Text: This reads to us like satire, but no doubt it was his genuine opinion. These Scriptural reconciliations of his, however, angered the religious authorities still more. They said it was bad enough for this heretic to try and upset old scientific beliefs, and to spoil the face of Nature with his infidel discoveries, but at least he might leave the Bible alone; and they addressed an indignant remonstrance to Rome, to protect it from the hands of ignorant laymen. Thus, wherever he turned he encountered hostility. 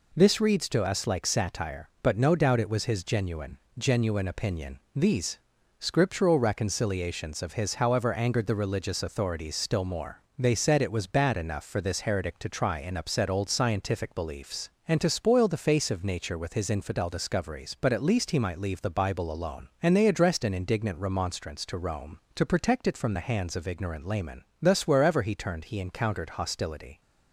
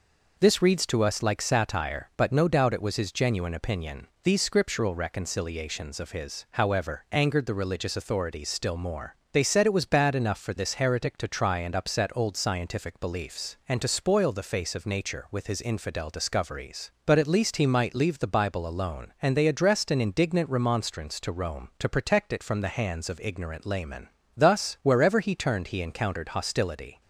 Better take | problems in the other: second | says "genuine" twice; at 3.7 s // pauses between "These" and "Scriptural"; at 5.3 s; 0.40 s long

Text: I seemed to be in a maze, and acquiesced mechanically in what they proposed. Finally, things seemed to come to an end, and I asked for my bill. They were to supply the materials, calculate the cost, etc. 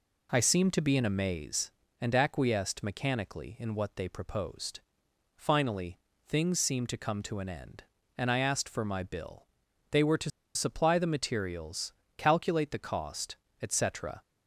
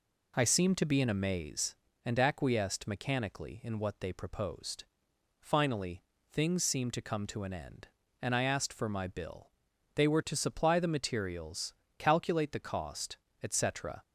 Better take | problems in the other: second | pauses between "to" and "supply"; slight; at 10.3 s; 0.25 s long

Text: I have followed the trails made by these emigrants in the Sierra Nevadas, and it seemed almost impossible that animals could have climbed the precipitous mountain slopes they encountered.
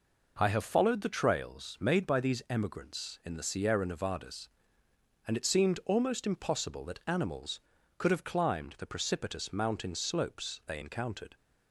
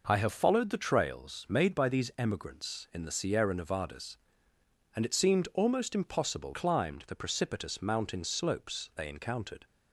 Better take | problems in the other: first | skips "that animals could have"; at 6.5 s

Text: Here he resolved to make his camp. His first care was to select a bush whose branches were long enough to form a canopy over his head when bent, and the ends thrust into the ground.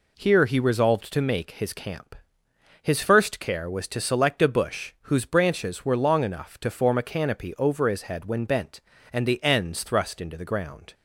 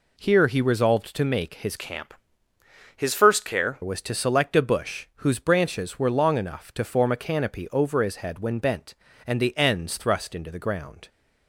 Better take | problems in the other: first | changes voice from "camp" to "care"; from 1.7 to 3.7 s; 2.0 s long

